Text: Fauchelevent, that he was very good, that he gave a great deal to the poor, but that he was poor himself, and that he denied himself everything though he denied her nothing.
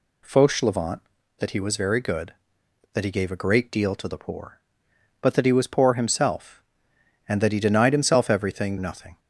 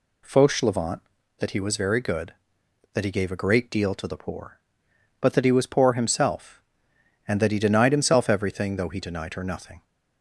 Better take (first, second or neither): second